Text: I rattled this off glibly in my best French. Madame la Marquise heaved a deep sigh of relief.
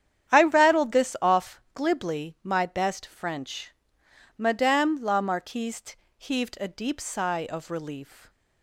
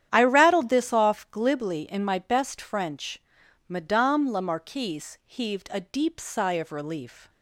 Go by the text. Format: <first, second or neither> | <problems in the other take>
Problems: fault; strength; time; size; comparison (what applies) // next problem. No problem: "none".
second | starts louder than the rest; strong; until 1.3 s; 9.5 dB; strong in the second // skips "in"; at 2.3 s // pauses between "Marquise" and "heaved"; slight; at 5.9 s; 0.22 s long